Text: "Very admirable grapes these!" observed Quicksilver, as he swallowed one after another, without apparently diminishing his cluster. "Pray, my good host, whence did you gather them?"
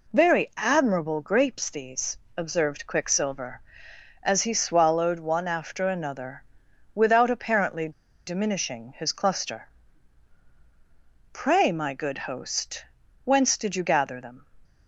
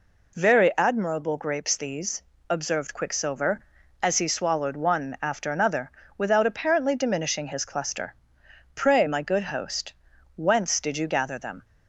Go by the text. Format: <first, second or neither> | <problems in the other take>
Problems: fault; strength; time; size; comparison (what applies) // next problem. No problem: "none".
second | pauses between "apparently" and "diminishing"; at 7.8 s; 0.36 s long